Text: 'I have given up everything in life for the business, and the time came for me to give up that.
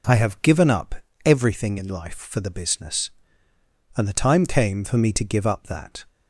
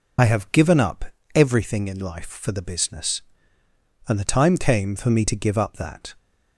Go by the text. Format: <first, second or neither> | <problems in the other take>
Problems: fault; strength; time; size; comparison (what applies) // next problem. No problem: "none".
first | loses the start of "I"; at 0.1 s; 45 ms // pauses between "up" and "everything"; slight; at 1.0 s; 0.28 s long; slight in the first